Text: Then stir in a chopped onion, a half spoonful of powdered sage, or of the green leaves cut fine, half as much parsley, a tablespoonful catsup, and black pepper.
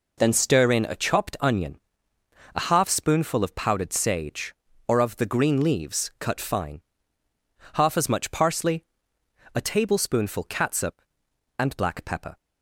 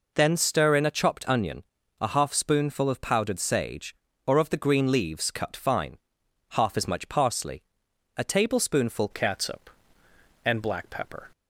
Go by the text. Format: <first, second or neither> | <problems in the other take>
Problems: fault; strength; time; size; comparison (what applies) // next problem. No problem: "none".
first | changes voice at "catsup"; from 9.1 s on; 2.1 s long